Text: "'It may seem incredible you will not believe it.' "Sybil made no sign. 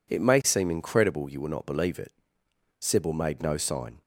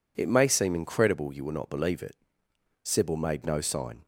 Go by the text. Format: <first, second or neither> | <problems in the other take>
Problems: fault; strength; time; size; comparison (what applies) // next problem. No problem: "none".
neither | none